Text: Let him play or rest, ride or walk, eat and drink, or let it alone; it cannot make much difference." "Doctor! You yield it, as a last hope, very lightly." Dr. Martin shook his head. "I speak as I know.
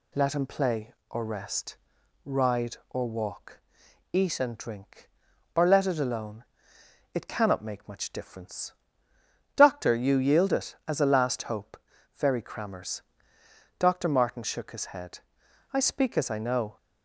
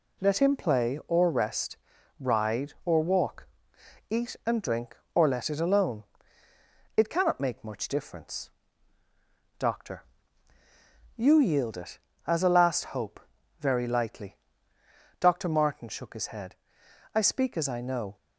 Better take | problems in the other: second | says "crammers" for "lightly"; at 12.4 s

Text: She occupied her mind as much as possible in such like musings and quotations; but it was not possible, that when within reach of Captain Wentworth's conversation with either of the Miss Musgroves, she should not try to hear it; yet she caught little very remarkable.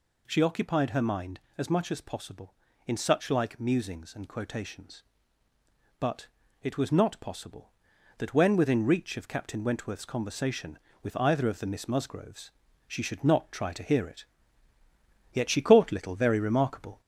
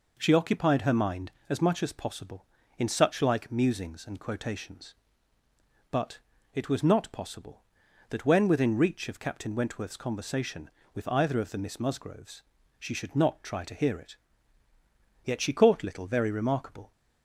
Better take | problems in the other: second | gets louder; slight; throughout; 2.5 dB // pauses between "but" and "it"; at 6.2 s; 0.38 s long; also in the second

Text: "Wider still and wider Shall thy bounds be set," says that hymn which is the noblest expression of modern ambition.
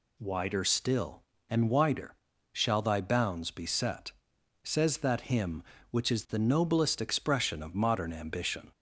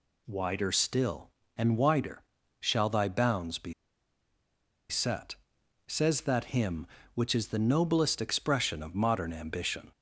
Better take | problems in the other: first | pauses between "wider" and "Shall"; slight; at 2.2 s; 0.36 s long; slight in the first // pauses between "be" and "set"; at 3.7 s; 1.1 s long

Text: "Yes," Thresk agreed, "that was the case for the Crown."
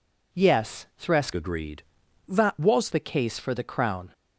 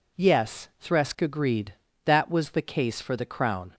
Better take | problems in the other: second | changes voice from "agreed" to "was"; from 1.3 to 2.8 s; 1.5 s long

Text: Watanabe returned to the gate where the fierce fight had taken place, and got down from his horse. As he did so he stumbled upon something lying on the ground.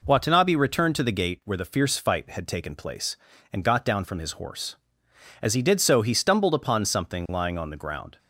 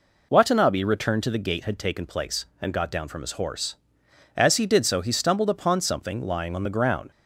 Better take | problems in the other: first | skips "where the fierce fight"; at 1.6 s

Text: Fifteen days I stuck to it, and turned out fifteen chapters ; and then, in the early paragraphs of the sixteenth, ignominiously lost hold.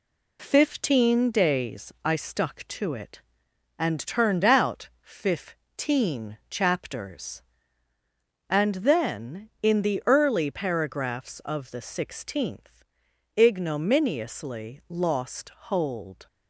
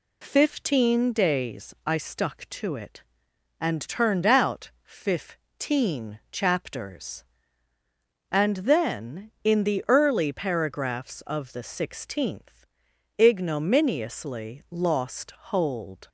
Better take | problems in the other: second | gets quieter; slight; throughout; 3 dB

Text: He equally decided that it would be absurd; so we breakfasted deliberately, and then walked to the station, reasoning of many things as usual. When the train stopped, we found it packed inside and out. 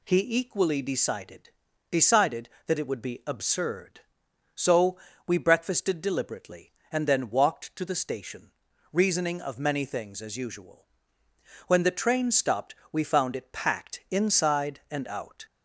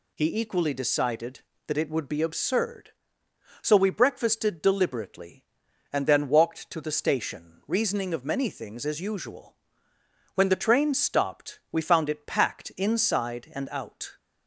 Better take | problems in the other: second | says "decided" twice; at 1.8 s // pauses between "so" and "we"; slight; at 4.9 s; 0.28 s long

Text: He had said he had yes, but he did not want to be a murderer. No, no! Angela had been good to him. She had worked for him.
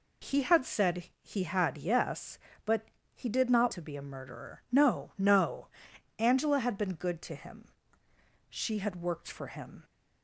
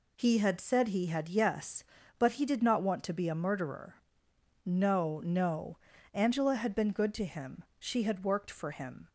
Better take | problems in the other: second | pauses between "but" and "he"; slight; at 2.8 s; 0.28 s long // skips "want"; at 3.7 s

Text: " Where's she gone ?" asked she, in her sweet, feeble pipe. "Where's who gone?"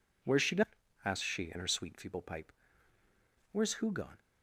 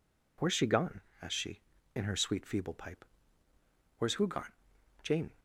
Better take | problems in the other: first | goes on to say "Jane"; slight; from 5.0 s on; 0.28 s long

